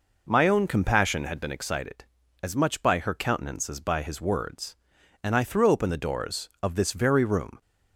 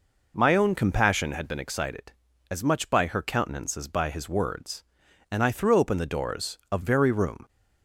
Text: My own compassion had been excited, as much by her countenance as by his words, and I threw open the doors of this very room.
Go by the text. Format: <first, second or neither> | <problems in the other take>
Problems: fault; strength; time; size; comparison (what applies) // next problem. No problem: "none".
first | skips "this"; at 6.8 s